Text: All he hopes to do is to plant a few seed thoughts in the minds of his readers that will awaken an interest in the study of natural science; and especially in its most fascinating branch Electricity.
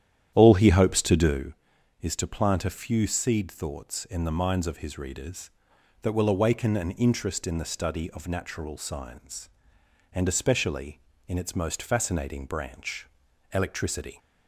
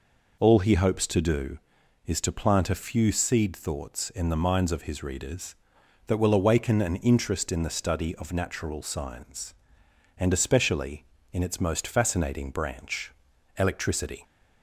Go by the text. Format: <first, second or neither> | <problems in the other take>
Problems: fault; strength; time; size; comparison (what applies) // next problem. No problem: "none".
second | starts louder than the rest; strong; until 1.5 s; 10.5 dB // pauses between "branch" and "Electricity"; noticeable; at 13.0 s; 0.46 s long; noticeable in the second